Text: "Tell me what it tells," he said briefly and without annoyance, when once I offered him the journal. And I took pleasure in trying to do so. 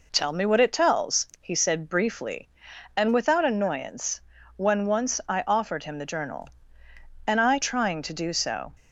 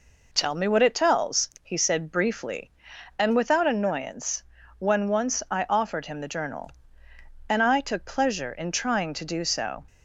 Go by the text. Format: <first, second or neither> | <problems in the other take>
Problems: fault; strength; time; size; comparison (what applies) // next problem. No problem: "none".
second | skips "took pleasure in"; at 7.5 s